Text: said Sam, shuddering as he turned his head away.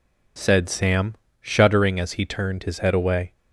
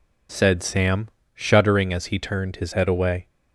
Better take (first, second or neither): neither